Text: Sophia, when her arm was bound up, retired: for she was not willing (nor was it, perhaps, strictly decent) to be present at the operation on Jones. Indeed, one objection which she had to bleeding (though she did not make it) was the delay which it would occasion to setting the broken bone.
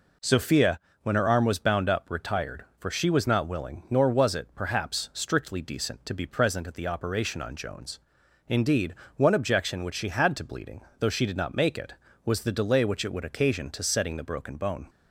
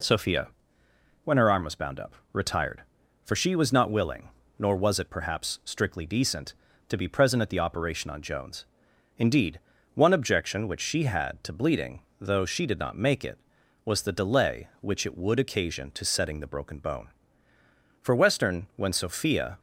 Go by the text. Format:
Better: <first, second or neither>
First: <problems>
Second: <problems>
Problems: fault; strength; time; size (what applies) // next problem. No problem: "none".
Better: first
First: none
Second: goes on to say "For Western when Sophia"; from 17.9 s on; 1.6 s long